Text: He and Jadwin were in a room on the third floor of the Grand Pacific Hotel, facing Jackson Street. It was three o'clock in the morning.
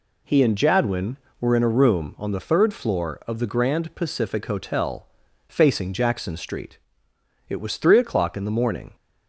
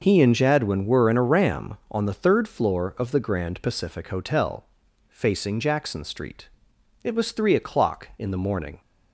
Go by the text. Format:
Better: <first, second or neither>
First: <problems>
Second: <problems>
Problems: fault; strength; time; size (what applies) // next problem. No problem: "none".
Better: first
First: none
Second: says "ram" for "room"; at 1.2 s